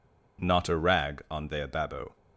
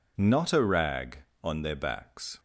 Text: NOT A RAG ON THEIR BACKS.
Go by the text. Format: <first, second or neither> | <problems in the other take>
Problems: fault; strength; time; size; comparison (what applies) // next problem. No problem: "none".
second | says "Babo" for "BACKS"; at 1.6 s